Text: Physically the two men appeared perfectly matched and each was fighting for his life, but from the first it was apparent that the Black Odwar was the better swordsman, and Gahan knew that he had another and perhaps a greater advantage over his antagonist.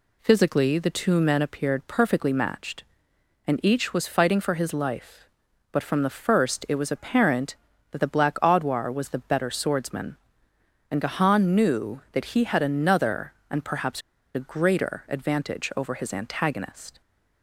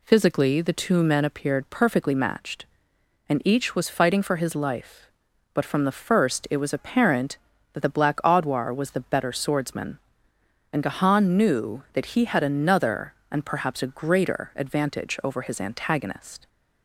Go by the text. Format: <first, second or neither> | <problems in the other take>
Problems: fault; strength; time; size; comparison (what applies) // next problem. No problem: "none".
second | pauses between "perhaps" and "a"; slight; at 14.0 s; 0.35 s long